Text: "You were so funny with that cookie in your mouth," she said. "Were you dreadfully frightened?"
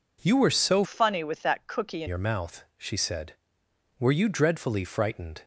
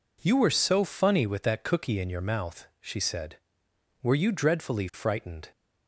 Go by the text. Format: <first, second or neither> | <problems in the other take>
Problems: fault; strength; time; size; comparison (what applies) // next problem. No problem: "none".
second | changes voice from "funny" to "in"; from 0.8 to 2.0 s; 1.2 s long